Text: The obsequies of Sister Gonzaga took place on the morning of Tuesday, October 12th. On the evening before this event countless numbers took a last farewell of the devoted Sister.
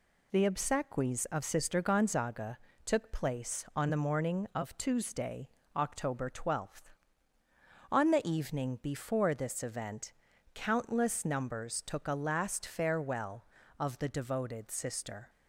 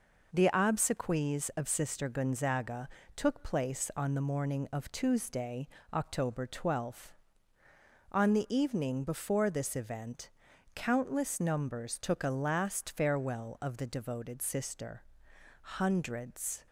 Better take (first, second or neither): first